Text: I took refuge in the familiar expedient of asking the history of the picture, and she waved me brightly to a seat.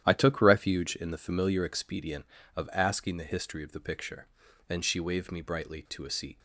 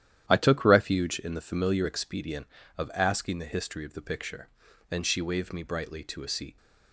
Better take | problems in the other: neither | starts louder than the rest; strong; the same in both

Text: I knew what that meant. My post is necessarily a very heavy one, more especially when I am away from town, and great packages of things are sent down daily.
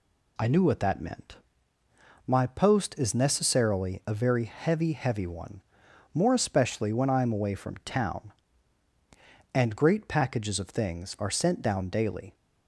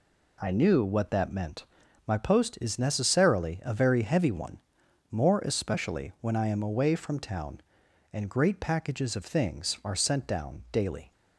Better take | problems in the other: second | says "heavy" twice; at 4.9 s

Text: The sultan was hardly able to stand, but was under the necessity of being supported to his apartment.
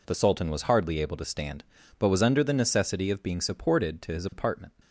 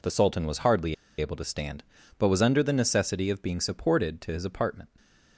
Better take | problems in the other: first | pauses between "hardly" and "able"; slight; at 0.9 s; 0.25 s long // stays silent after the last word; slight; from 4.8 s on; 0.5 s long

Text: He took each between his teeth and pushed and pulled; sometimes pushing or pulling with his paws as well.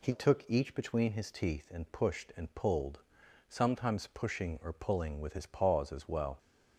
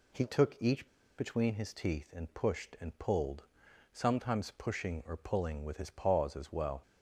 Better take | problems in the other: first | pauses between "each" and "between"; slight; at 0.8 s; 0.31 s long

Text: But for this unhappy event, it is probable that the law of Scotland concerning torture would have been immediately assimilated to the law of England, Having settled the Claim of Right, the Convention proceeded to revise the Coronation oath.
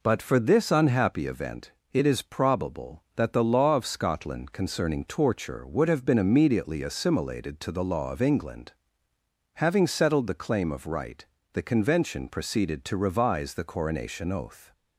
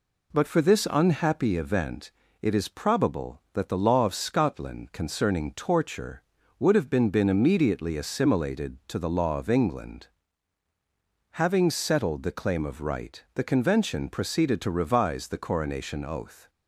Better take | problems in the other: first | says "been" twice; at 7.0 s

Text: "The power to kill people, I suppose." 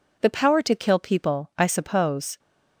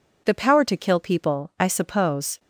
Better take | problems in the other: neither | none

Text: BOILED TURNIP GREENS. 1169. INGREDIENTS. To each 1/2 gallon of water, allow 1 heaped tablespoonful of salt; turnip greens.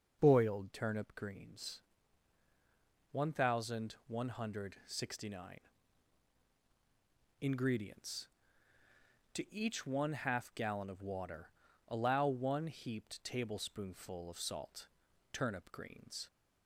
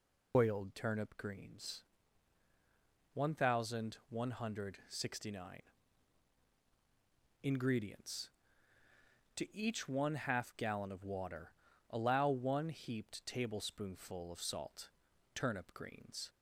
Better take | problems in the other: first | loses the start of "BOILED"; at 0.3 s; 120 ms

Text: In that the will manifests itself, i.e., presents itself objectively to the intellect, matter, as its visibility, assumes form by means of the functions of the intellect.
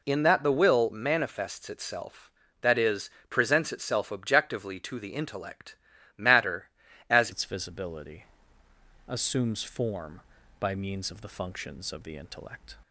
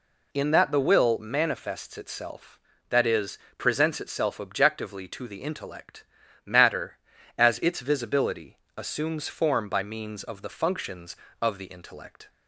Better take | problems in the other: second | changes voice at "its"; from 7.3 s on; 5.4 s long

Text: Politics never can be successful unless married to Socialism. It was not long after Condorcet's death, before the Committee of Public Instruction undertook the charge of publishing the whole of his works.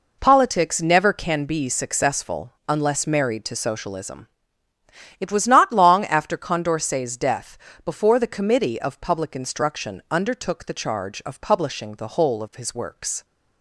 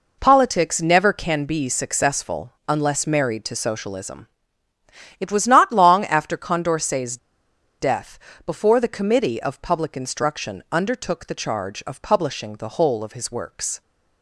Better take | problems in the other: first | pauses between "Condorcet's" and "death"; noticeable; at 7.1 s; 0.64 s long

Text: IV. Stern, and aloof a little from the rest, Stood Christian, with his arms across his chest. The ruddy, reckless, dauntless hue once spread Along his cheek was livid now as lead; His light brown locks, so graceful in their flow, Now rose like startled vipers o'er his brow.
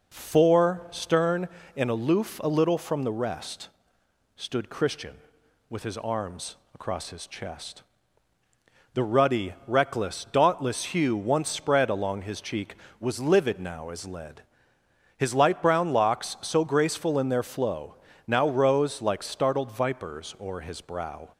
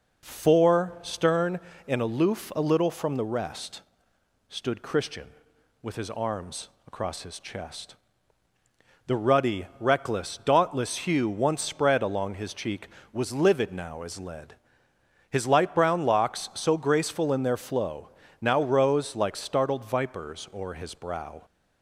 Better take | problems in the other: neither | pauses between "arms" and "across"; slight; the same in both

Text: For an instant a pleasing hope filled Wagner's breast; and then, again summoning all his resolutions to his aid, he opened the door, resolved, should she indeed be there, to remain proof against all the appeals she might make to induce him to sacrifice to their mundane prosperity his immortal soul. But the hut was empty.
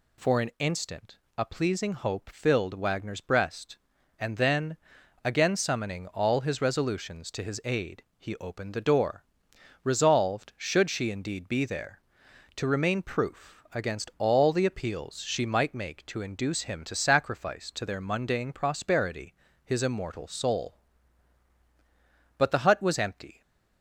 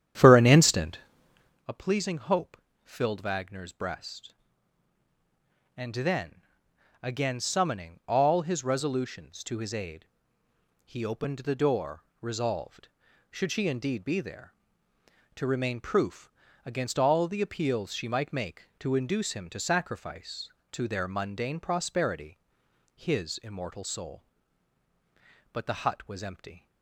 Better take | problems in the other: first | starts louder than the rest; strong; until 1.7 s; 10.5 dB // pauses between "instant" and "a"; noticeable; at 1.0 s; 0.68 s long; slight in the first // pauses between "hope" and "filled"; slight; at 2.5 s; 0.30 s long // pauses between "proof" and "against"; slight; at 16.3 s; 0.34 s long // pauses between "prosperity" and "his"; noticeable; at 22.3 s; 0.56 s long; slight in the first

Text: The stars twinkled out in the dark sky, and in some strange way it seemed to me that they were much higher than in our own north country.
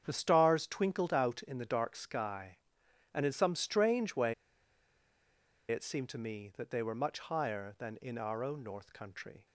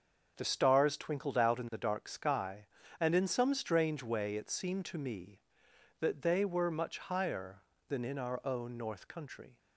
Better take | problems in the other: second | starts louder than the rest; strong; until 1.0 s; 8 dB; also in the second // pauses between "way" and "it"; strong; at 4.3 s; 1.3 s long

